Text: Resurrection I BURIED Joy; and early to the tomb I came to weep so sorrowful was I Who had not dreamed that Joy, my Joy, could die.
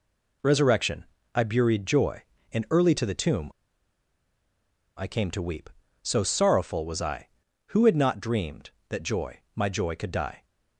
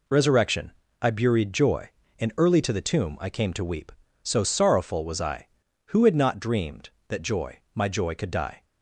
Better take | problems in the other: second | pauses between "Resurrection" and "I"; slight; at 1.0 s; 0.32 s long; slight in the second // pauses between "tomb" and "I"; strong; at 3.4 s; 1.4 s long

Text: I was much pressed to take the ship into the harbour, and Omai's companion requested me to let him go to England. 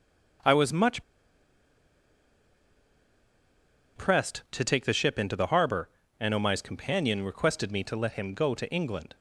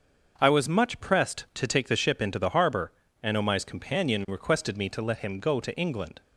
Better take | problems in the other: second | starts louder than the rest; until 4.3 s; 6.5 dB; also in the second // pauses between "much" and "pressed"; strong; at 1.0 s; 2.9 s long

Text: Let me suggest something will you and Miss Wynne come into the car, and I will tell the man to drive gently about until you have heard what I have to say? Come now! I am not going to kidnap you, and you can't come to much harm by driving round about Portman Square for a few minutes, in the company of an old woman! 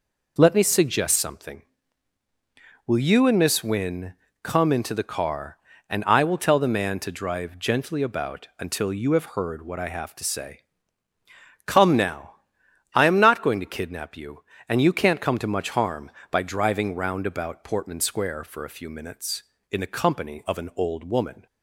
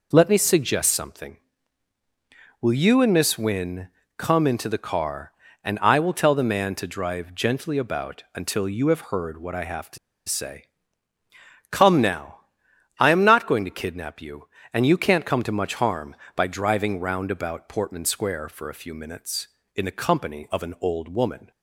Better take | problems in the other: first | pauses between "Wynne" and "come"; slight; at 3.8 s; 0.28 s long; slight in the first // pauses between "to" and "say"; slight; at 9.9 s; 0.30 s long

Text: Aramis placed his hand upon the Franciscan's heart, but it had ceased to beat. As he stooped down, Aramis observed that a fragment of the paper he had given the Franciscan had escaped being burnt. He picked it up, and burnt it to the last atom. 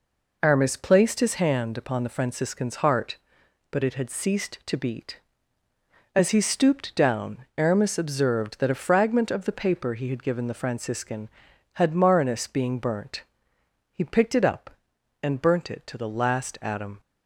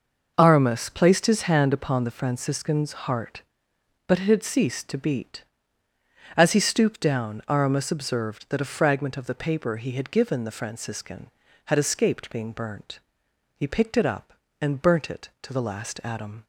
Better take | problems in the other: second | says "marinus" for "escaped"; at 11.9 s

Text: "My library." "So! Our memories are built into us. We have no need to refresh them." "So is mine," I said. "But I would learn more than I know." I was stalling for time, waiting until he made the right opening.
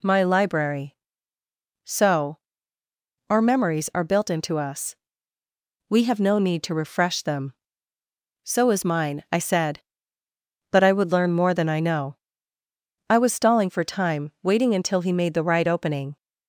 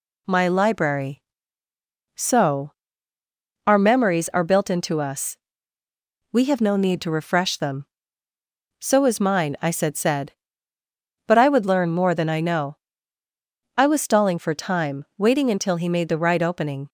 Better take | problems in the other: first | says "said" twice; at 9.9 s

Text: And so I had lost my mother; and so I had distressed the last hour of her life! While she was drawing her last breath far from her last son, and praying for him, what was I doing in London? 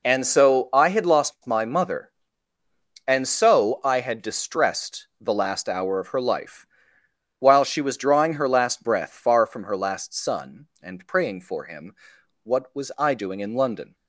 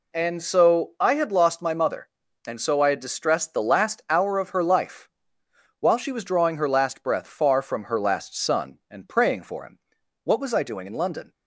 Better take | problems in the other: neither | none

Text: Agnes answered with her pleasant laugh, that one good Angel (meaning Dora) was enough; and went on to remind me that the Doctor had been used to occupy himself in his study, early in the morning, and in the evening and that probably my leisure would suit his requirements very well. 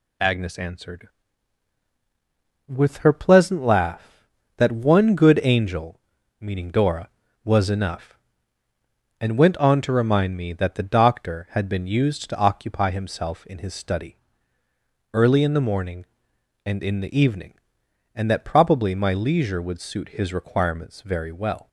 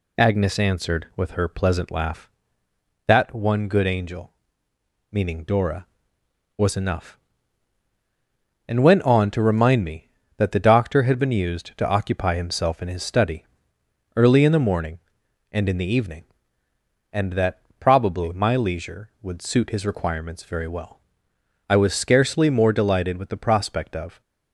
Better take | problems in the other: first | pauses between "that" and "probably"; slight; at 17.6 s; 0.18 s long // goes on to say "I was scarcely more delighted with the prospect of"; strong; from 21.6 s on; 2.5 s long

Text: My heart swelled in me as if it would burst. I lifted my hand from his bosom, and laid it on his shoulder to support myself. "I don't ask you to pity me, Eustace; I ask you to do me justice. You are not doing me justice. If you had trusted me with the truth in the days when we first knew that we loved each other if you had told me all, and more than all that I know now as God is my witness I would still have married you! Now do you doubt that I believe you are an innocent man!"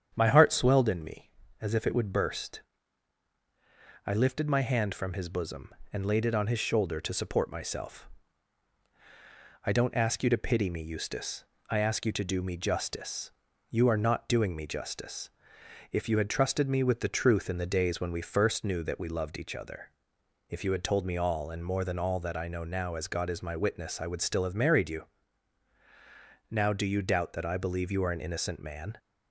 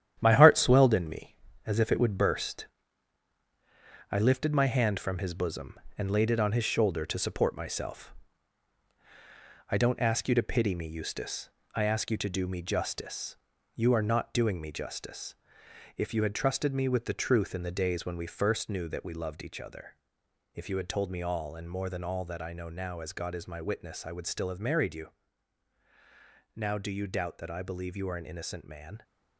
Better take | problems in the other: first | gets quieter; strong; throughout; 8 dB // starts louder than the rest; strong; until 1.2 s; 10 dB; strong in the first // pauses between "other" and "if"; noticeable; at 19.9 s; 0.60 s long; noticeable in the first

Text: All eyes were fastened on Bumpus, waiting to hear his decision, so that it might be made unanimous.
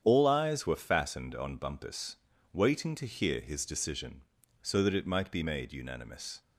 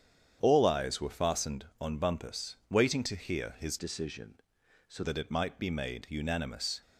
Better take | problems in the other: first | starts louder than the rest; strong; until 1.4 s; 8.5 dB; strong in the first // changes voice from "decision" to "so"; from 3.7 to 5.0 s; 1.3 s long

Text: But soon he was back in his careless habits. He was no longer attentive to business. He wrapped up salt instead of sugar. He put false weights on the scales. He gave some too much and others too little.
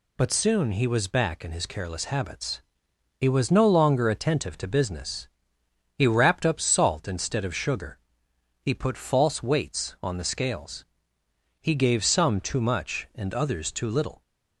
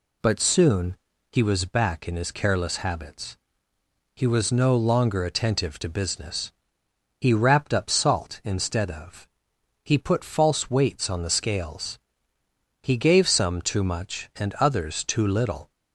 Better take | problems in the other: first | pauses between "soon" and "he"; slight; at 0.9 s; 0.36 s long // skips "sugar"; at 9.5 s

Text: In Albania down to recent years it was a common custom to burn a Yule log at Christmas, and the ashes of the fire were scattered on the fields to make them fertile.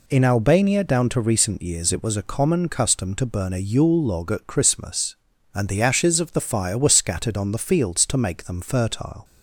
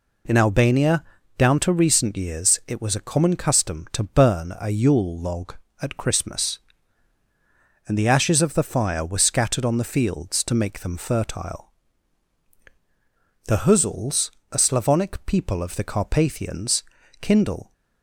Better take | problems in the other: first | pauses between "Albania" and "down"; slight; at 1.0 s; 0.34 s long // goes on to say "The Huzuls a Slavonic people of the Carpathians kindle"; strong; from 13.4 s on; 4.2 s long

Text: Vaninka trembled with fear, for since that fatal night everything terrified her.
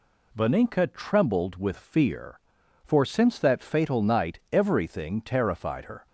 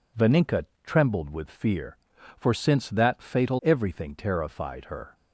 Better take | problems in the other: first | pauses between "Vaninka" and "trembled"; slight; at 0.6 s; 0.18 s long // skips "night"; at 3.6 s

